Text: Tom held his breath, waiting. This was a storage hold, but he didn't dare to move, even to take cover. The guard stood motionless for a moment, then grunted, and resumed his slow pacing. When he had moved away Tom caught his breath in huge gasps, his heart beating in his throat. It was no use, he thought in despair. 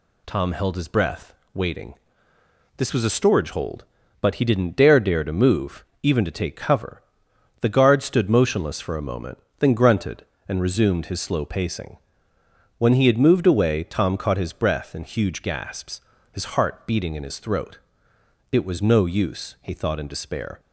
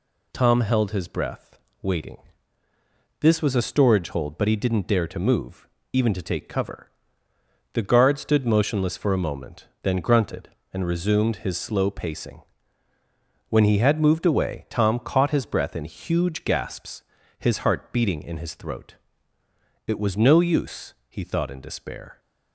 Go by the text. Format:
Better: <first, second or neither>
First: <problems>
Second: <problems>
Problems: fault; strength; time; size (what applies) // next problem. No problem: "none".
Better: second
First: says "dare" twice; at 4.9 s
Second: none